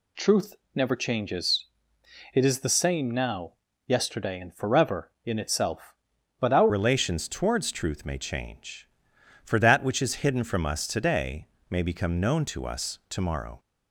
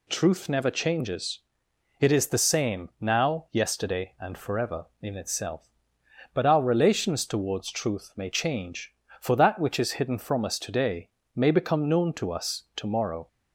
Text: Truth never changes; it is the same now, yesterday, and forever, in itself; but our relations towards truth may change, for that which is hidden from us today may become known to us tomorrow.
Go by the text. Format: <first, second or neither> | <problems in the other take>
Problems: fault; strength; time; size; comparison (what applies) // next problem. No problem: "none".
second | pauses between "Truth" and "never"; slight; at 0.5 s; 0.20 s long // changes voice at "relations"; from 6.6 s on; 6.9 s long // pauses between "today" and "may"; slight; at 11.4 s; 0.24 s long; slight in the second